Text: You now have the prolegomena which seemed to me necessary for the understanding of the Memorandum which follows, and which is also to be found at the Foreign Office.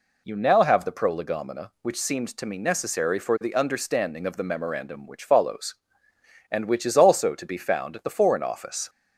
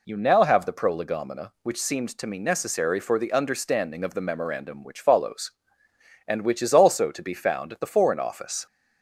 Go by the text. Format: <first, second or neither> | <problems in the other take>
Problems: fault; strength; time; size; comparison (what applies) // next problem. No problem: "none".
neither | none